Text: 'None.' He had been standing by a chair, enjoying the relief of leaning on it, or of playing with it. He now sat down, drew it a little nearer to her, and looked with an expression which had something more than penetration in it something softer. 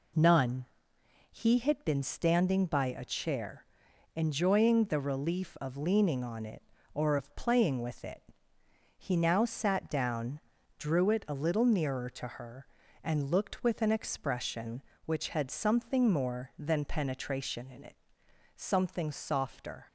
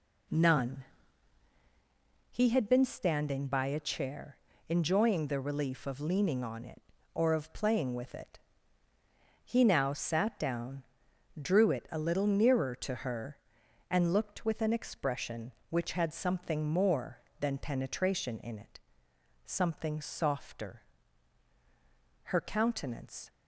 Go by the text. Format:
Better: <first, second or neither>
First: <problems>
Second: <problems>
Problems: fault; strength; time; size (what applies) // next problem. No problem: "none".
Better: first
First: pauses between "it" and "something"; noticeable; at 17.9 s; 0.60 s long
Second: pauses between "it" and "something"; noticeable; at 18.7 s; 0.68 s long // goes on to say "Her countenance"; noticeable; from 22.2 s on; 1.0 s long